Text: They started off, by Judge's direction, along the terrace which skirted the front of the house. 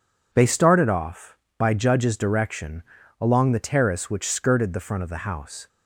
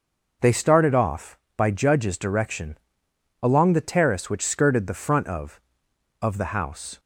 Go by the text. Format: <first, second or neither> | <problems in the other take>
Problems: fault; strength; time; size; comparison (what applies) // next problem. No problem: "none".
first | says "of" twice; at 6.2 s